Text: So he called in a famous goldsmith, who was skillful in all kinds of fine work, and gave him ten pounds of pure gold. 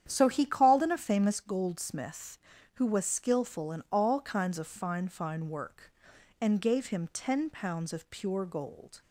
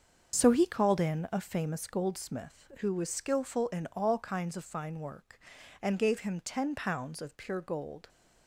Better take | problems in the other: second | starts louder than the rest; strong; until 1.0 s; 9.5 dB; also in the second // says "fine" twice; at 5.0 s

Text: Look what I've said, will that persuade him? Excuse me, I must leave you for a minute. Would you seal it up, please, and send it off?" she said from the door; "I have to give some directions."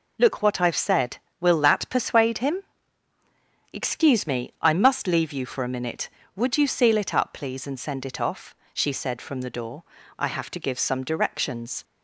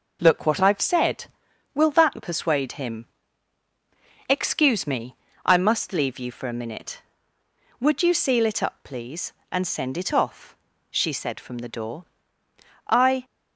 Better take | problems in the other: first | stops before "have to give some directions"; at 13.2 s

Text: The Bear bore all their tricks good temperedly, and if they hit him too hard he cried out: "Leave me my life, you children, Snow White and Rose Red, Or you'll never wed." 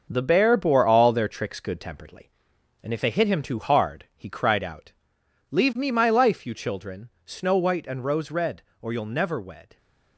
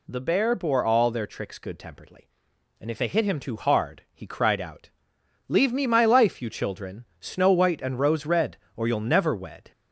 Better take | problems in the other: second | gets quieter; throughout; 7 dB

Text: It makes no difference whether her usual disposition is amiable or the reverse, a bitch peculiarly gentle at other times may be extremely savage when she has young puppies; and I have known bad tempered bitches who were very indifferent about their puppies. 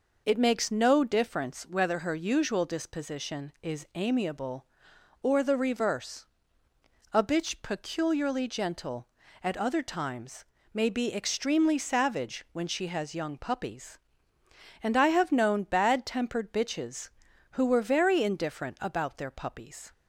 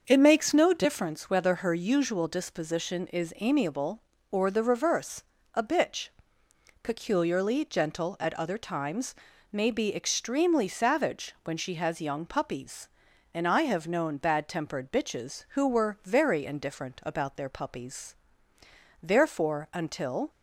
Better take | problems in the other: first | starts louder than the rest; until 1.0 s; 6.5 dB // pauses between "bitch" and "peculiarly"; noticeable; at 6.0 s; 0.74 s long // pauses between "times" and "may"; slight; at 9.1 s; 0.36 s long; slight in the first // goes on to say "Therefore until"; noticeable; from 19.0 s on; 1.2 s long

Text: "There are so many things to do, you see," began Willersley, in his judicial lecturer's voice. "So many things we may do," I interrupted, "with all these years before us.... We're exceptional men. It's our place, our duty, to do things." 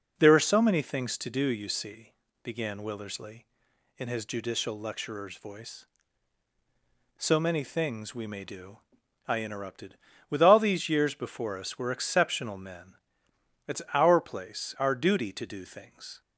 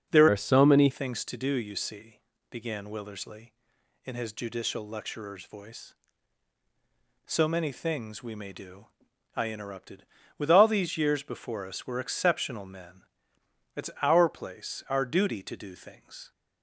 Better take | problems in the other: first | changes voice from "are" to "many"; from 0.3 to 0.8 s; 0.5 s long

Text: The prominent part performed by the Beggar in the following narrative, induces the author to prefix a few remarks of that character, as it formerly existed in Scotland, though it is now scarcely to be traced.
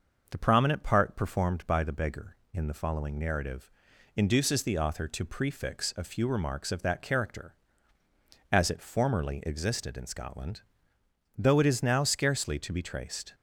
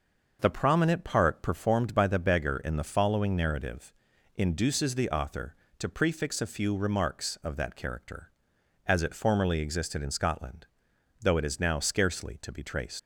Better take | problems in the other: first | starts louder than the rest; noticeable; until 1.4 s; 6 dB; noticeable in the first // leaves "traced" unfinished; at 12.9 s; 105 ms

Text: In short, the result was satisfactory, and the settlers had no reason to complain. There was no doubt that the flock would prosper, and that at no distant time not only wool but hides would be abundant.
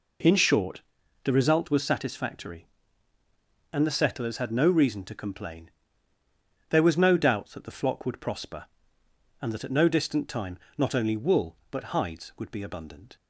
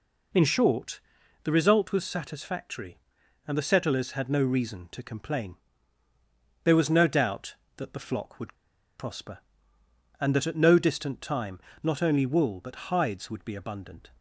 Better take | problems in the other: first | pauses between "would" and "prosper"; at 8.5 s; 0.44 s long // pauses between "time" and "not"; slight; at 11.5 s; 0.24 s long; slight in the first

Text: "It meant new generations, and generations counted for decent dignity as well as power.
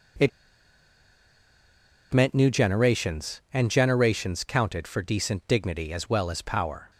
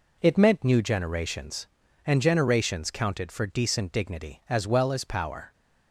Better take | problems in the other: second | pauses between "It" and "meant"; strong; at 0.2 s; 1.8 s long

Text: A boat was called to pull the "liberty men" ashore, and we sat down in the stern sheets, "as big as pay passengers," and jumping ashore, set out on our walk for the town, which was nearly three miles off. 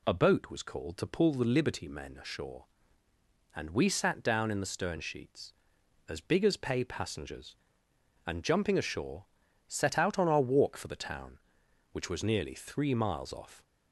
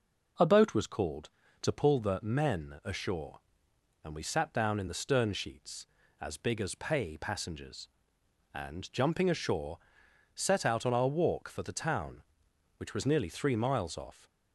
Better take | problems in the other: first | skips "liberty"; at 2.1 s

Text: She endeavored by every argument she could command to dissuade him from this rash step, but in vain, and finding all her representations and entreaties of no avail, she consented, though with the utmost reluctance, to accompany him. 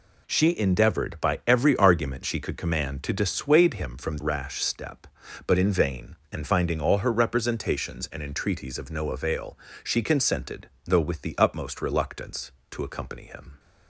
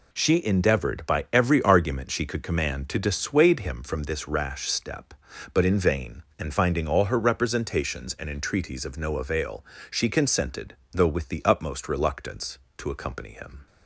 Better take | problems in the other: second | skips "this"; at 4.1 s

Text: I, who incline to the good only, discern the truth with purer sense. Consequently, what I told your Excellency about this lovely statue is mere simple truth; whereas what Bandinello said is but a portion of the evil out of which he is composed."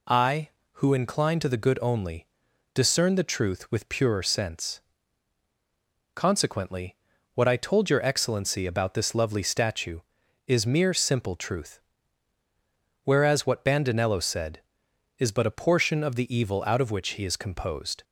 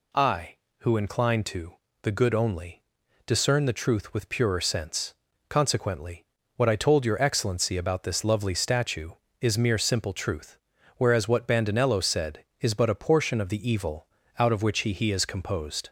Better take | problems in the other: first | pauses between "to" and "the"; slight; at 1.7 s; 0.28 s long // pauses between "evil" and "out"; slight; at 14.0 s; 0.32 s long // says "he" twice; at 14.9 s

